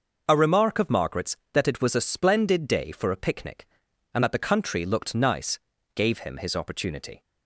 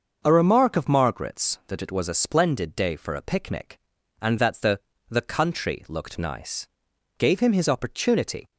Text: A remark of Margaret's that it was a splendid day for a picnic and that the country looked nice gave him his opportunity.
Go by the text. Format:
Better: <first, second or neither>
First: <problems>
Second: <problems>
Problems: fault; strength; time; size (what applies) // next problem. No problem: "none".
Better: first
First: pauses between "nice" and "gave"; slight; at 5.5 s; 0.36 s long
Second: starts louder than the rest; until 1.2 s; 6.5 dB // says "the" twice; at 5.0 s // pauses between "nice" and "gave"; noticeable; at 6.6 s; 0.52 s long